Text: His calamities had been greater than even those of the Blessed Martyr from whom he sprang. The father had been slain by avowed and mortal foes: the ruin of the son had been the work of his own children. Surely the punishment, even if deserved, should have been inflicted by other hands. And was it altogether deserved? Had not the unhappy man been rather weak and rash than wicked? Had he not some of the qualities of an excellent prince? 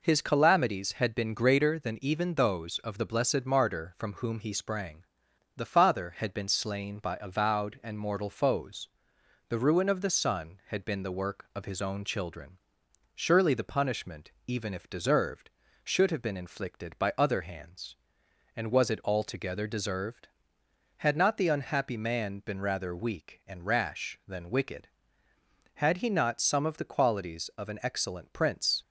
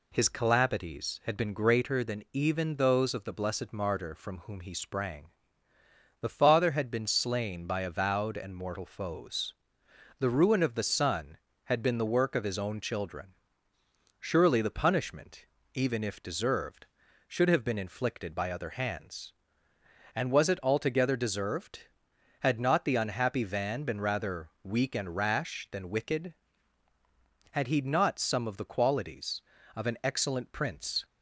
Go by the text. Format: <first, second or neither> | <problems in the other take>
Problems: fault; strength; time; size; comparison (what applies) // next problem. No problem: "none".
first | says "van" for "man"; at 23.4 s